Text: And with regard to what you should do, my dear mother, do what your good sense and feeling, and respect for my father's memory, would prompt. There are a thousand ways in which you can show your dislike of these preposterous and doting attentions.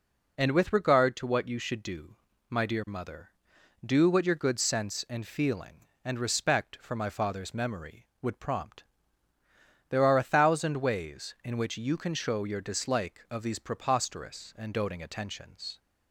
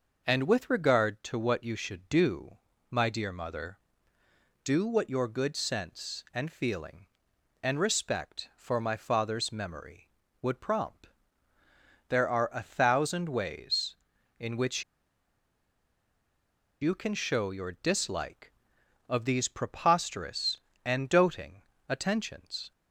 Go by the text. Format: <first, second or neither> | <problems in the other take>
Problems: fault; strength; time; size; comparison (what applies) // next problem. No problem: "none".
first | pauses between "which" and "you"; strong; at 14.8 s; 1.9 s long // pauses between "doting" and "attentions"; slight; at 21.6 s; 0.26 s long